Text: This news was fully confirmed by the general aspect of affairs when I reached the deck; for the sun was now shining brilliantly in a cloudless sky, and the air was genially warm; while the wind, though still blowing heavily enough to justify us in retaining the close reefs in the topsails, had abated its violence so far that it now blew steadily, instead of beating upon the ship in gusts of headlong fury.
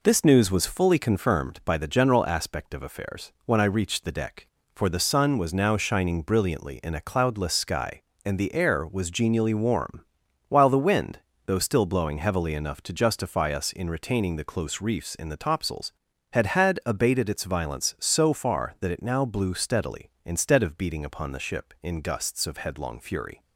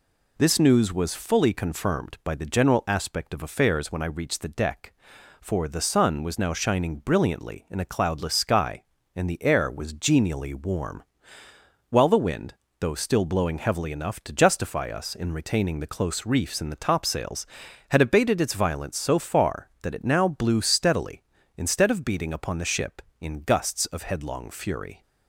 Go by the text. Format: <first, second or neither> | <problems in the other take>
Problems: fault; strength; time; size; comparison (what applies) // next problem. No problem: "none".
second | says "had" twice; at 16.4 s